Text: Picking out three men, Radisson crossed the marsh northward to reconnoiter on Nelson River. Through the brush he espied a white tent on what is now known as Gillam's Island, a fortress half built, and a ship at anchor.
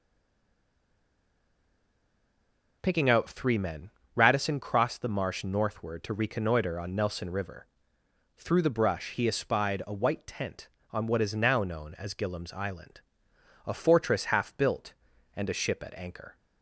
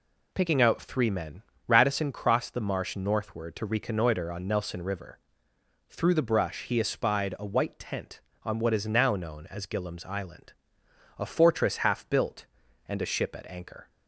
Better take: second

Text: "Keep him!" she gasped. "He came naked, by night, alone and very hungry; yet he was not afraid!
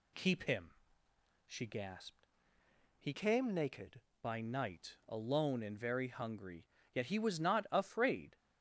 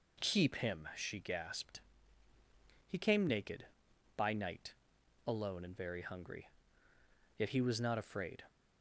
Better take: second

